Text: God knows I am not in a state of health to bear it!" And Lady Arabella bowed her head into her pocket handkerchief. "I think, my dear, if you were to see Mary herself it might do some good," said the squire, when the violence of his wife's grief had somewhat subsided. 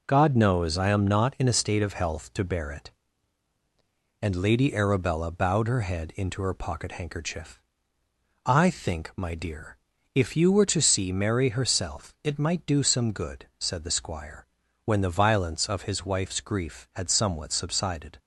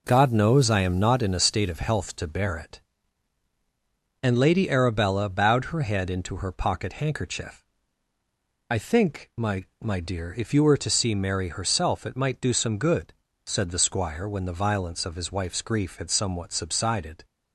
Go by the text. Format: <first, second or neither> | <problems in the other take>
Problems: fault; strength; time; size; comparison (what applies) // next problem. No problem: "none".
first | says "my" twice; at 9.8 s